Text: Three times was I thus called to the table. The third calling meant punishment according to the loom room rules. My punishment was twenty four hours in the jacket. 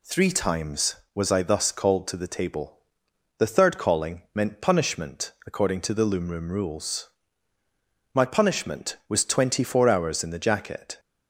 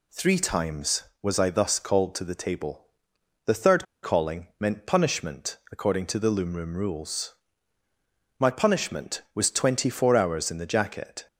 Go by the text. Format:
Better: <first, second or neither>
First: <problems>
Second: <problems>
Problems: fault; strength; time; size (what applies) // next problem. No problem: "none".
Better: first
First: none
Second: pauses between "third" and "calling"; slight; at 3.8 s; 0.17 s long